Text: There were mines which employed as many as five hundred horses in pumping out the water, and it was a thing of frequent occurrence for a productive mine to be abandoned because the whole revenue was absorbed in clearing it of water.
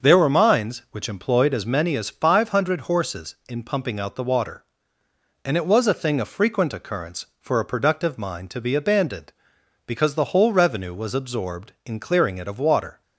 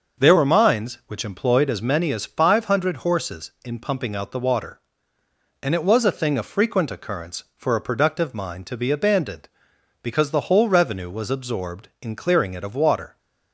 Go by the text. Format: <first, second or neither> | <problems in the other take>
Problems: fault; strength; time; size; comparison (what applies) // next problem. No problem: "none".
neither | starts louder than the rest; the same in both